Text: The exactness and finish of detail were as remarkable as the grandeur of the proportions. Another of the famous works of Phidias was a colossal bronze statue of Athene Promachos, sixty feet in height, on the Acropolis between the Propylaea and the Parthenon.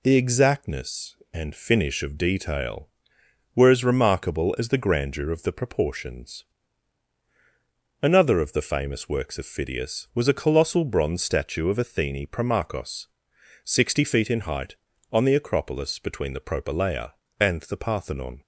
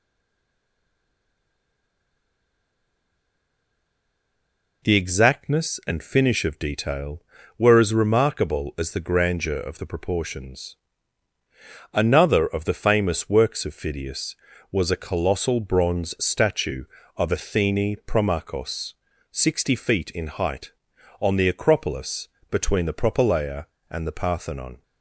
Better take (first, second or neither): first